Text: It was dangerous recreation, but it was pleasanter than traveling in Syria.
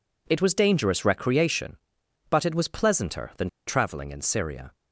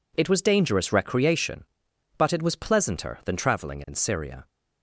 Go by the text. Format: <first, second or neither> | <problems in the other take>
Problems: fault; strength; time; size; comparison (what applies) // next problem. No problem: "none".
second | pauses between "than" and "traveling"; slight; at 3.4 s; 0.20 s long